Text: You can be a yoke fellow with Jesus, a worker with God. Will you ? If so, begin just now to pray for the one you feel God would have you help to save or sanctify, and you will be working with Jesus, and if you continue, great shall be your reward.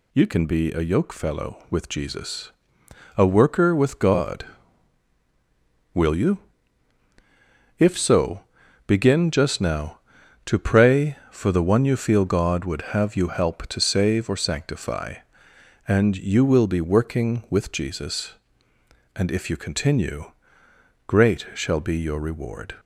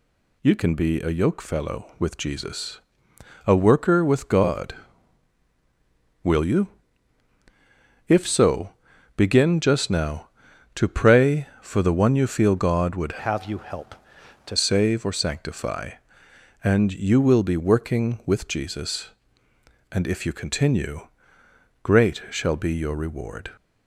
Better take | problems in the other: first | changes voice from "have" to "to"; from 13.1 to 14.5 s; 1.4 s long

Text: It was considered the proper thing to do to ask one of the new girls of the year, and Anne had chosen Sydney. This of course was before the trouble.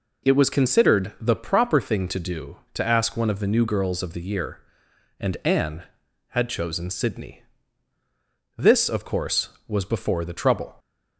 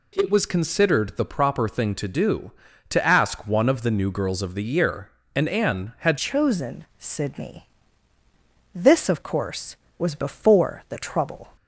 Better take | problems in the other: first | changes voice at "chosen"; from 6.1 s on; 5.4 s long // pauses between "chosen" and "Sydney"; slight; at 6.8 s; 0.16 s long

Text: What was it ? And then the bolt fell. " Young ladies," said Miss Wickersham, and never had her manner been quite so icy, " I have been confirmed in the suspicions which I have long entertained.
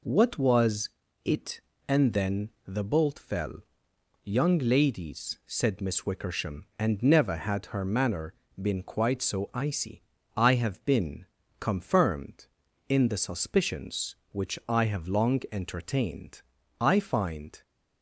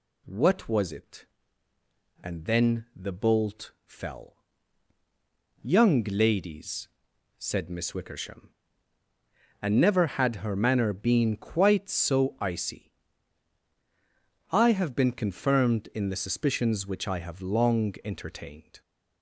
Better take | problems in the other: second | pauses between "was" and "it"; slight; at 0.8 s; 0.36 s long // pauses between "then" and "the"; slight; at 2.4 s; 0.18 s long // pauses between "manner" and "been"; slight; at 8.3 s; 0.28 s long // pauses between "been" and "confirmed"; slight; at 11.2 s; 0.34 s long // goes on to say "I find"; noticeable; from 16.8 s on; 0.82 s long

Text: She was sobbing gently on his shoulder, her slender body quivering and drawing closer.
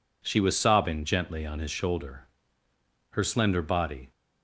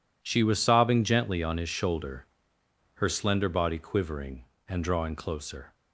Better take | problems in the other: second | stops before "quivering and drawing closer"; at 4.1 s

